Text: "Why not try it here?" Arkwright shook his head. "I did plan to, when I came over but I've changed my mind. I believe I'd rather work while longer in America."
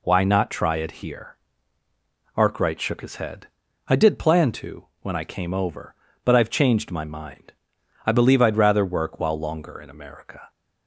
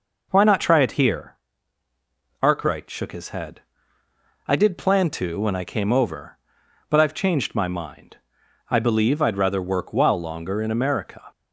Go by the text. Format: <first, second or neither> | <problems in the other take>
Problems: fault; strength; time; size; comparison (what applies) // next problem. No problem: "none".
neither | none